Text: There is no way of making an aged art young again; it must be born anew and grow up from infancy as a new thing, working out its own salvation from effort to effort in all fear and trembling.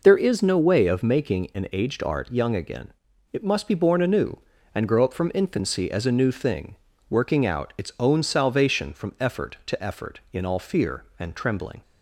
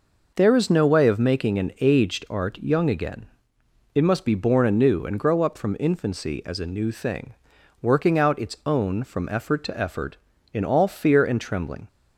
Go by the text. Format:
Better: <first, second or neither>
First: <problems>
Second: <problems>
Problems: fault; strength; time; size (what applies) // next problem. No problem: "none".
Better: first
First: none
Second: skips "salvation"; at 9.0 s